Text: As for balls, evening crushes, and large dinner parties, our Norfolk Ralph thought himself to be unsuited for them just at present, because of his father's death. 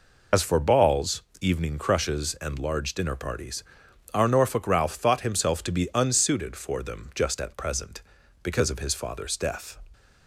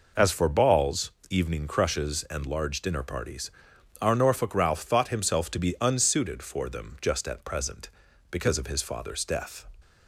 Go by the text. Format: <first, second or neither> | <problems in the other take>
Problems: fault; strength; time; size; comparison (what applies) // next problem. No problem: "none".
second | loses the start of "As"; at 0.3 s; 65 ms